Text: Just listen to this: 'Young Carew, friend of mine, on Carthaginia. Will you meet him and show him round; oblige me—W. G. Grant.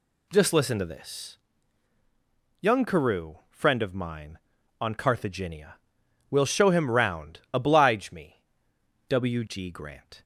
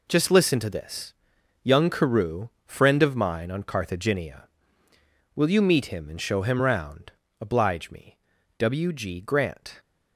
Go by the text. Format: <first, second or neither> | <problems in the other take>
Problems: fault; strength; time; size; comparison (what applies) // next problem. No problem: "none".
second | skips "you meet him and"; at 6.4 s